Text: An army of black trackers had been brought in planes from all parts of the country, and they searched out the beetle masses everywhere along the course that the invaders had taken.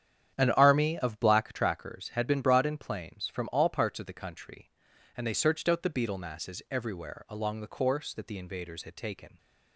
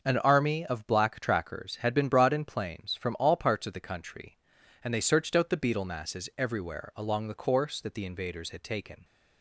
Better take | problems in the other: second | starts louder than the rest; strong; until 1.5 s; 9 dB

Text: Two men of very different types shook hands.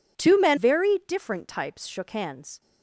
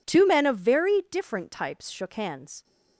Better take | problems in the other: second | skips "of"; at 0.5 s

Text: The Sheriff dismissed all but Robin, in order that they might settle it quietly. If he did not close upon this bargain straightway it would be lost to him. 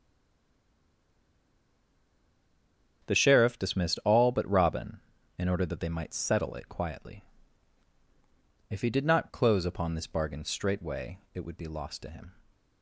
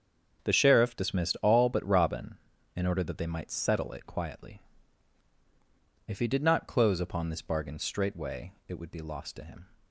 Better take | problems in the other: second | stays silent before the first word; strong; until 3.0 s; 3.0 s long // starts louder than the rest; strong; until 4.1 s; 8 dB; strong in the second

